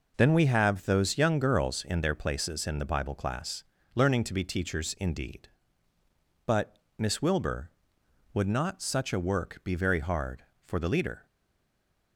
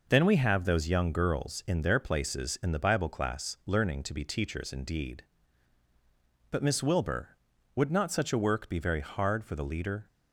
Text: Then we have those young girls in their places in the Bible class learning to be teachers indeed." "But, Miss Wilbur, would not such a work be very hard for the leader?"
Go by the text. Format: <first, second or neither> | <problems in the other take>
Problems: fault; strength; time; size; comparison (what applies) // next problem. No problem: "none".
second | pauses between "class" and "learning"; slight; at 3.6 s; 0.32 s long // stays silent after the last word; slight; from 11.2 s on; 0.9 s long